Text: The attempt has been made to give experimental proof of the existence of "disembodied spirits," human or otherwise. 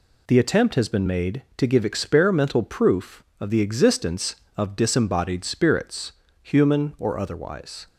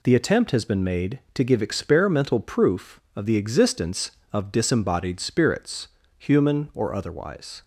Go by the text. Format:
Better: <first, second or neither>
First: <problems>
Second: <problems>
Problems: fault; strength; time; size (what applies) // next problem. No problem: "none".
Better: neither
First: none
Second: none